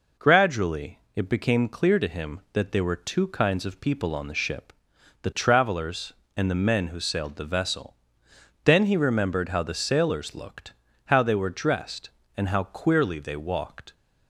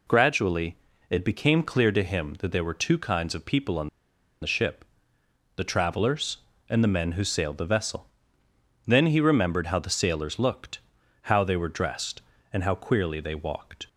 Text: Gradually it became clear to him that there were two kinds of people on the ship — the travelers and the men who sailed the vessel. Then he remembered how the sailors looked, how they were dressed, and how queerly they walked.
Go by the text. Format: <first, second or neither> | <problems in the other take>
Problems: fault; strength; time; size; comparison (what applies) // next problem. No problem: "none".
first | pauses between "Gradually" and "it"; slight; at 0.7 s; 0.34 s long; slight in the first // pauses between "on" and "the"; noticeable; at 3.8 s; 0.53 s long